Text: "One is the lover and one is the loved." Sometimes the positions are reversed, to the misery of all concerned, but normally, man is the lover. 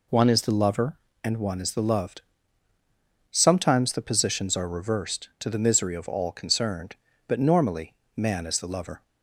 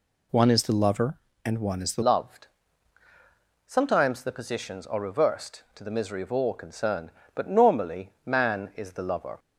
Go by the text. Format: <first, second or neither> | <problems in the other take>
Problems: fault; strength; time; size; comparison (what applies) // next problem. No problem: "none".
first | changes voice at "loved"; from 2.0 s on; 7.3 s long